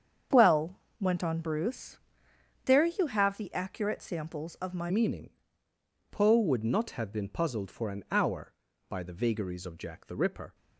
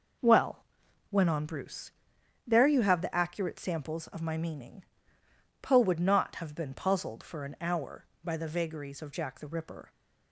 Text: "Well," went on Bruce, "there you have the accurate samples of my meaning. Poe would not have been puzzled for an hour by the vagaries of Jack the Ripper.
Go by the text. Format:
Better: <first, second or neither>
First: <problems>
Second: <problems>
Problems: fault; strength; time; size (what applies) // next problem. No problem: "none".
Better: second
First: starts louder than the rest; strong; until 1.5 s; 7.5 dB // changes voice at "meaning"; from 4.8 s on; 5.7 s long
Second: none